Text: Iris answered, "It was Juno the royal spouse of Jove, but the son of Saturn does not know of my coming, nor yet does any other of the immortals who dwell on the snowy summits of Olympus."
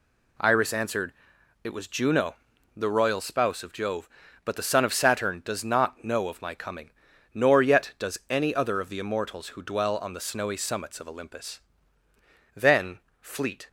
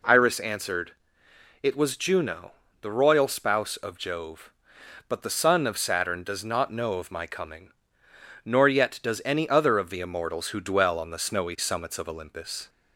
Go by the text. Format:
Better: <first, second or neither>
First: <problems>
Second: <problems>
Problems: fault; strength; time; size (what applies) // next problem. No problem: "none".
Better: second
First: pauses between "Juno" and "the"; at 2.3 s; 0.44 s long // goes on to say "Then fleet"; noticeable; from 12.5 s on; 1.1 s long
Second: pauses between "Juno" and "the"; slight; at 2.5 s; 0.28 s long